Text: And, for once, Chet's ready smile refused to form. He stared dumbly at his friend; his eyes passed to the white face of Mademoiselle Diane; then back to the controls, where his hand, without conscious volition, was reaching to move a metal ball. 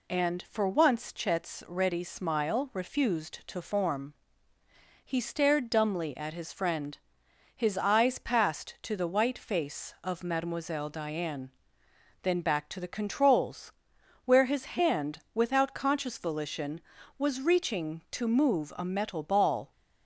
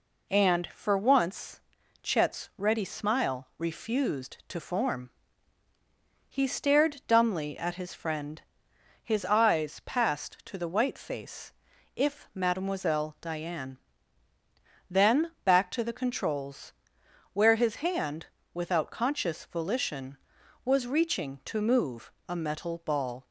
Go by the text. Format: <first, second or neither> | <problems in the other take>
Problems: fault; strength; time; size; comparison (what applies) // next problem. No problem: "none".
first | says "if" for "of"; at 11.9 s // pauses between "move" and "a"; slight; at 22.1 s; 0.16 s long